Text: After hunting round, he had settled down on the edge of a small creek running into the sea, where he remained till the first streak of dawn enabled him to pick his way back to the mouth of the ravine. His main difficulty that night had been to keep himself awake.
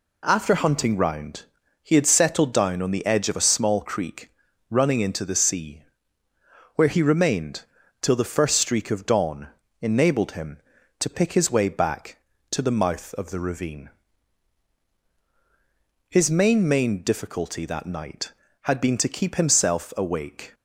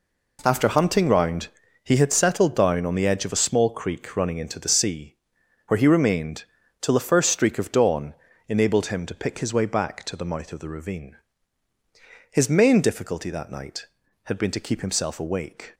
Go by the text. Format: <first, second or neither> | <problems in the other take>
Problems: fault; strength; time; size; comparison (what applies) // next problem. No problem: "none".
second | pauses between "creek" and "running"; at 4.2 s; 0.40 s long // pauses between "remained" and "till"; slight; at 7.6 s; 0.36 s long; slight in the second // pauses between "dawn" and "enabled"; slight; at 9.4 s; 0.34 s long; slight in the second // says "main" twice; at 16.6 s